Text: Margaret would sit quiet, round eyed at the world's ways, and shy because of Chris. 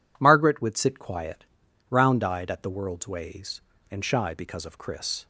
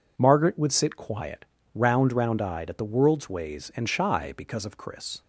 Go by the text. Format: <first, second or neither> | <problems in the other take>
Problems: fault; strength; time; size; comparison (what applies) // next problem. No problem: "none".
first | says "round" twice; at 2.1 s